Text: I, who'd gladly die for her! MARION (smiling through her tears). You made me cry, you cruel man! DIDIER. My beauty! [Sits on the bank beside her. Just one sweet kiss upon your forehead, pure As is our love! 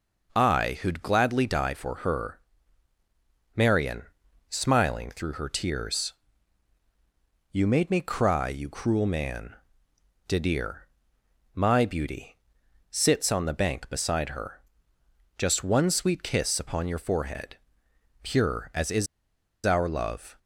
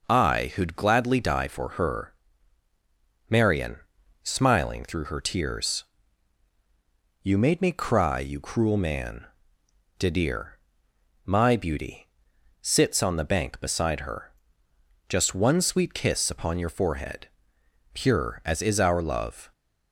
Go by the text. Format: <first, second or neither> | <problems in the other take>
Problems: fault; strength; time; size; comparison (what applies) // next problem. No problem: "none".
second | pauses between "is" and "our"; noticeable; at 19.0 s; 0.59 s long